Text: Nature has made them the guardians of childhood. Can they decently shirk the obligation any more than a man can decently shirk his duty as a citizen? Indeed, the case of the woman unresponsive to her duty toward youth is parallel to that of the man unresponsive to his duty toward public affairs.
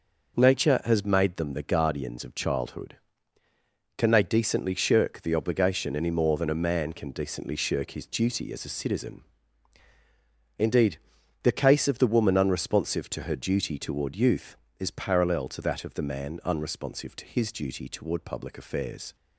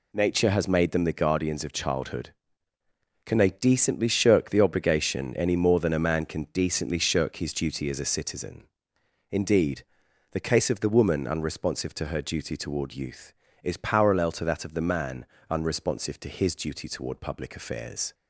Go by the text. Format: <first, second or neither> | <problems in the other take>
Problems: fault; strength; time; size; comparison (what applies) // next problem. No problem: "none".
first | gets quieter; strong; throughout; 9 dB // pauses between "man" and "unresponsive"; slight; at 15.2 s; 0.24 s long